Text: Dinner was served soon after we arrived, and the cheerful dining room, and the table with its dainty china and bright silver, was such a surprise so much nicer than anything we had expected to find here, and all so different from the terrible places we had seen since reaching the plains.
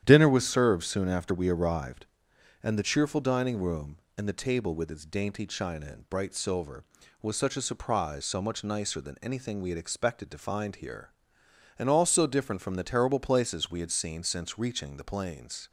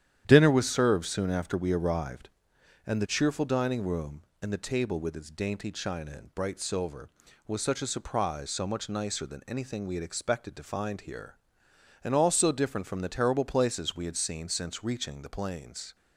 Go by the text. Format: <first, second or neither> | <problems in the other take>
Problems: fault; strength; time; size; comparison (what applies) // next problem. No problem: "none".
neither | starts louder than the rest; strong; the same in both